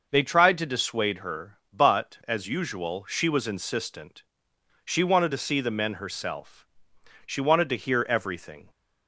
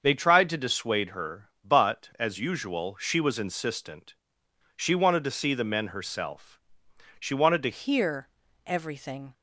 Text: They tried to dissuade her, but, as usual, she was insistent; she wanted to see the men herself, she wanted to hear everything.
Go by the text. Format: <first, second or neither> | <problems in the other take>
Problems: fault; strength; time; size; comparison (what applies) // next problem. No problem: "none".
first | starts louder than the rest; until 1.0 s; 6.5 dB // changes voice at "hear"; from 7.7 s on; 1.6 s long // pauses between "hear" and "everything"; at 8.2 s; 0.38 s long